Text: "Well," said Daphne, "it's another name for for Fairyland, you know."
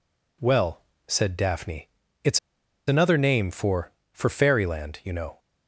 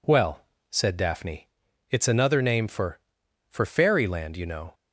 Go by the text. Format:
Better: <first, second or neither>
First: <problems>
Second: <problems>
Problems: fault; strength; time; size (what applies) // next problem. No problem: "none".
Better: second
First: pauses between "it's" and "another"; noticeable; at 2.3 s; 0.49 s long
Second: none